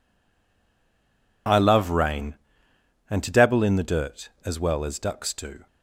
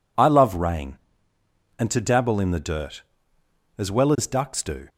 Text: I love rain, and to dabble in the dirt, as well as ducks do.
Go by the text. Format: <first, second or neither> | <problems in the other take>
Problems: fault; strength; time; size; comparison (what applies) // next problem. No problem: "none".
second | stays silent before the first word; noticeable; until 1.4 s; 1.4 s long